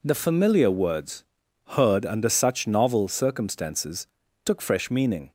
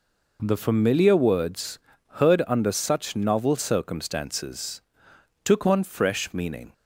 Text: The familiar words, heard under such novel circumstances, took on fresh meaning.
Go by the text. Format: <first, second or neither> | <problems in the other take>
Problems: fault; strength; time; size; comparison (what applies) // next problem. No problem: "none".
second | skips "on"; at 4.6 s